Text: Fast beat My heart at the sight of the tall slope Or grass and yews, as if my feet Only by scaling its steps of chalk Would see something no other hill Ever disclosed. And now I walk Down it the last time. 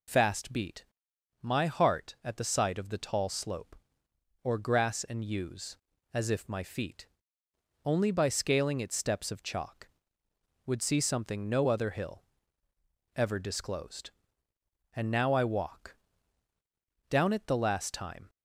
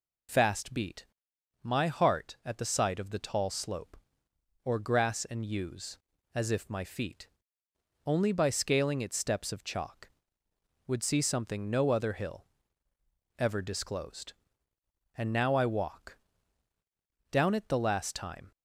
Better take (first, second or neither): neither